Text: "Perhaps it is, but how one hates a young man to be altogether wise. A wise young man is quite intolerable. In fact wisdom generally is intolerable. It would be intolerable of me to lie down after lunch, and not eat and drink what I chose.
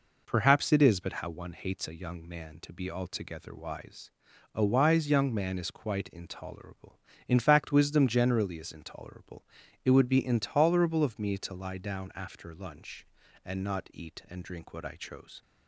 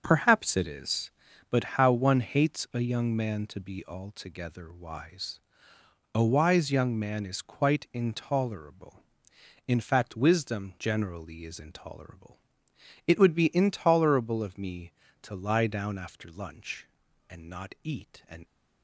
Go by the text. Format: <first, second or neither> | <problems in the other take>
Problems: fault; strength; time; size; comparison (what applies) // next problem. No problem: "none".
first | starts louder than the rest; until 1.0 s; 6 dB // pauses between "but" and "how"; slight; at 1.6 s; 0.18 s long // stops before "drink what I chose"; at 18.4 s